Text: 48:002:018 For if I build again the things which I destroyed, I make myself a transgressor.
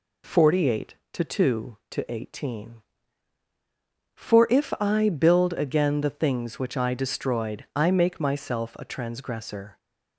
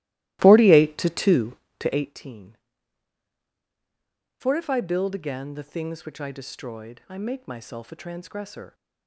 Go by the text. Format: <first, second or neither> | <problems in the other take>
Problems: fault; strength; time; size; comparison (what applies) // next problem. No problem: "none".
first | starts louder than the rest; strong; until 2.2 s; 17.5 dB